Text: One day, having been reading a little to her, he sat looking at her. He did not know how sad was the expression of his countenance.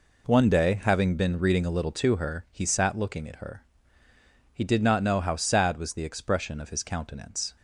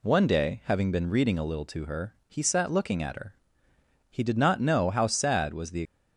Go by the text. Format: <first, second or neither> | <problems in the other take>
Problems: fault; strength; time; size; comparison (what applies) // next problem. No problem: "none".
first | stops before "expression of his countenance"; at 5.8 s